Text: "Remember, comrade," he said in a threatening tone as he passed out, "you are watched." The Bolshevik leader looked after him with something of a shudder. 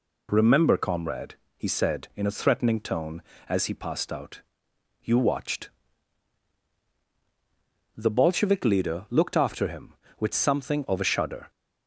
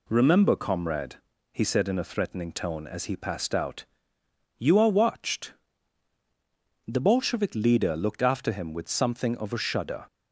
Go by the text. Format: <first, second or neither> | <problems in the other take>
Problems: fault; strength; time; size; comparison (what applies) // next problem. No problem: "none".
second | skips "are"; at 5.1 s